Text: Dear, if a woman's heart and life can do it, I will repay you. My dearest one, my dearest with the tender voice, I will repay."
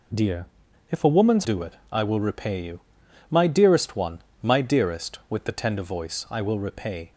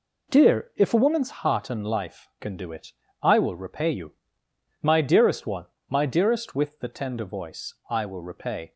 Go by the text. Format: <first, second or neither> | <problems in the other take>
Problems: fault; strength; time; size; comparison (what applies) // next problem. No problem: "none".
second | skips "heart and life can"; at 1.4 s